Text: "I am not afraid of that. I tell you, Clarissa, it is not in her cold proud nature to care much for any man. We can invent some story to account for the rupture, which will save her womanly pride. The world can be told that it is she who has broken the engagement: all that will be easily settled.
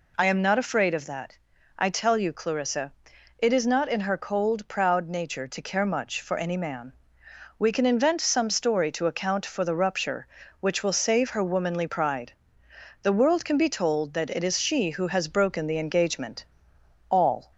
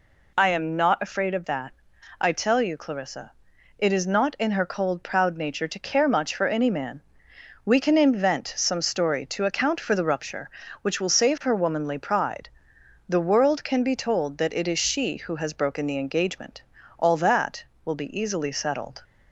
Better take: second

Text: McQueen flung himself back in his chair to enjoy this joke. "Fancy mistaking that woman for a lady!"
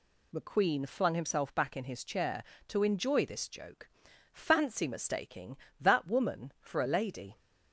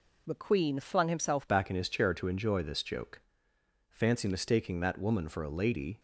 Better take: first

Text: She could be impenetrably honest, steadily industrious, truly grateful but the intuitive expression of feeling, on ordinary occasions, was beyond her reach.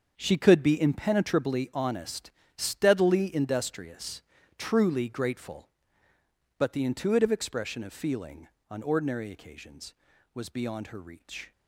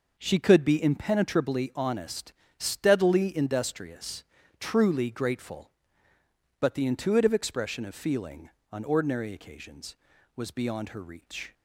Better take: second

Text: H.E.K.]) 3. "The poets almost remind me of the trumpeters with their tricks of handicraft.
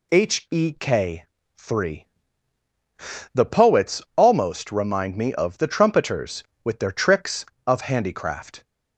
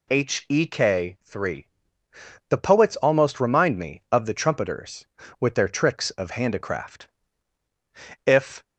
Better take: first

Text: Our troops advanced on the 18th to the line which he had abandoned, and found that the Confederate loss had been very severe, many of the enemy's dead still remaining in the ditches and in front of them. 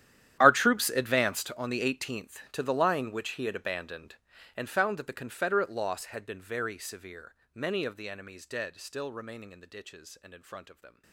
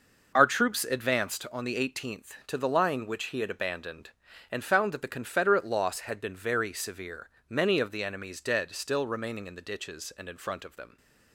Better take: second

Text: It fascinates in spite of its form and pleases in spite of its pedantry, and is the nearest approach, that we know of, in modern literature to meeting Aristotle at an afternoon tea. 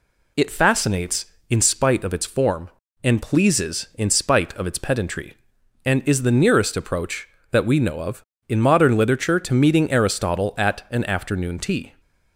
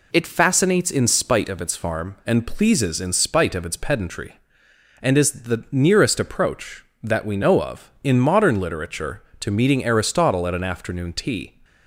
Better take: first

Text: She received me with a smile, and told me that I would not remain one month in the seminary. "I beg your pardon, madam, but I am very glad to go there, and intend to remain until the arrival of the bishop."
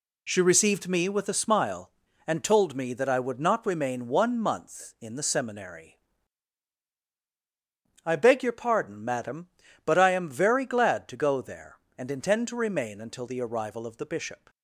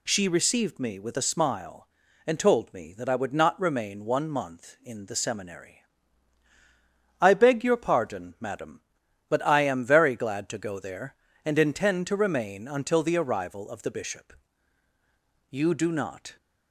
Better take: first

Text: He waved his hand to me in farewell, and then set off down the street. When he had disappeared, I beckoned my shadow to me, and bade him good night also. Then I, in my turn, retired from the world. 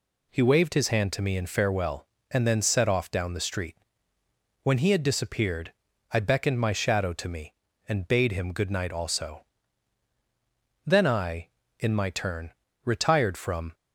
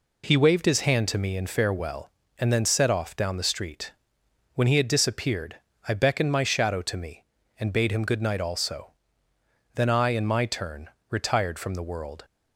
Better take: second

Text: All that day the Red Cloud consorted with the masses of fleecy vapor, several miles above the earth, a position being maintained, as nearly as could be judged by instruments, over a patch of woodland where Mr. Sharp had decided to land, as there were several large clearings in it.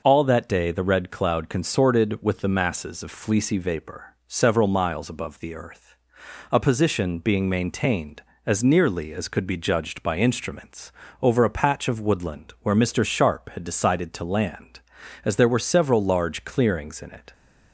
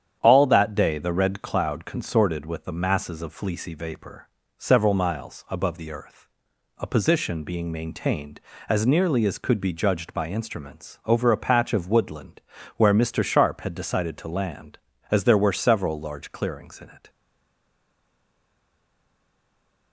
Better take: first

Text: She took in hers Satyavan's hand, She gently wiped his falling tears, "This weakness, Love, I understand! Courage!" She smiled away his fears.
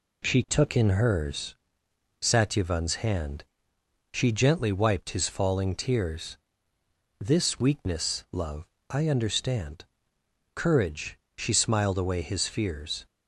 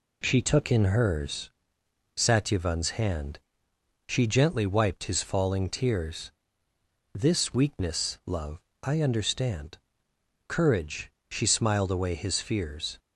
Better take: neither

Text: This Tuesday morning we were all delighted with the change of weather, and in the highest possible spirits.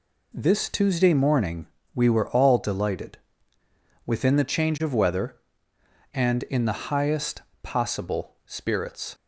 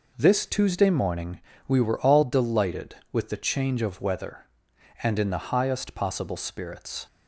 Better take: second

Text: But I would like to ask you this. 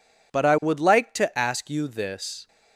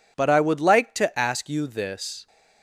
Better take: neither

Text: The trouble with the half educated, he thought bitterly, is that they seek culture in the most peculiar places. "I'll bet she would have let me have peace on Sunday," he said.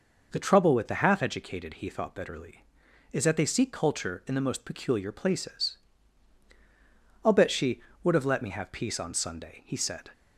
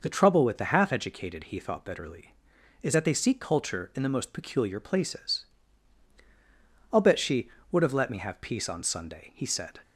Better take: neither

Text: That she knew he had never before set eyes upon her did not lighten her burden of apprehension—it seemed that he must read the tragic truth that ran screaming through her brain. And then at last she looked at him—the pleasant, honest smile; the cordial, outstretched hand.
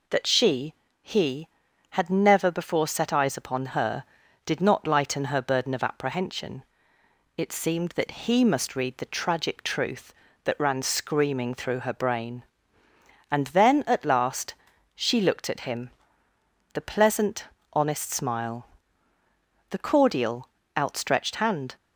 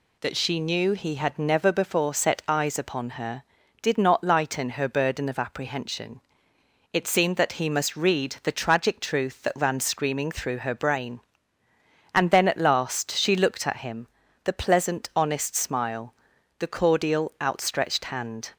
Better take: second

